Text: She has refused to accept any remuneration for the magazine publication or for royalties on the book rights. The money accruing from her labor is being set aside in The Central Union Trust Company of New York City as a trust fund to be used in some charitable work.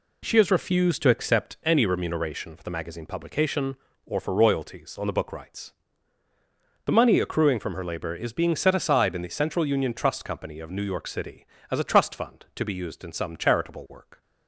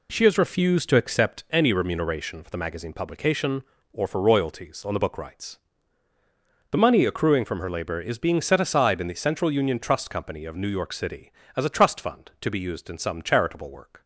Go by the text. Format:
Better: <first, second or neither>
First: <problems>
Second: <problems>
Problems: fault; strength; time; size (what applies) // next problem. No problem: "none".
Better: neither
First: none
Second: none